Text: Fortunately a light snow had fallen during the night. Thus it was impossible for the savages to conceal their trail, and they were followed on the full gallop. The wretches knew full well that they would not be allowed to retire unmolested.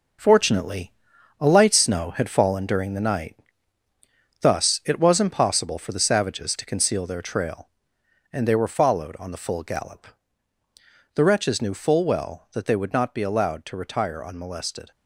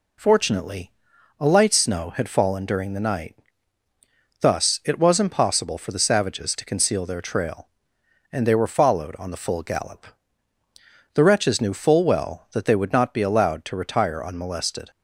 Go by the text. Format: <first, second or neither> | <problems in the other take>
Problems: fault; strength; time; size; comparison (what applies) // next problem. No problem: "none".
second | gets quieter; strong; throughout; 8 dB // pauses between "Fortunately" and "a"; noticeable; at 0.9 s; 0.48 s long; noticeable in the second